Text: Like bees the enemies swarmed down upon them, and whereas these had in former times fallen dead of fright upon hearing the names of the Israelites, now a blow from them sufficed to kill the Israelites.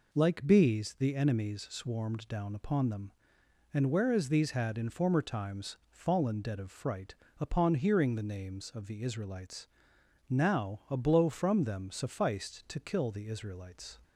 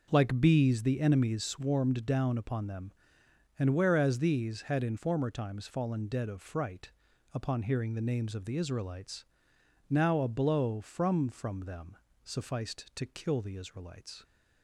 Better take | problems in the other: first | pauses between "fright" and "upon"; at 6.9 s; 0.42 s long; slight in the first // says "from" twice; at 11.2 s // pauses between "them" and "sufficed"; slight; at 11.9 s; 0.26 s long

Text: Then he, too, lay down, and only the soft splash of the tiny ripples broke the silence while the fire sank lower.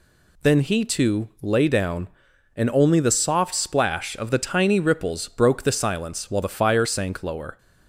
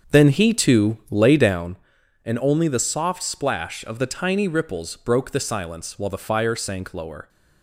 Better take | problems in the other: first | starts louder than the rest; strong; until 1.6 s; 7 dB

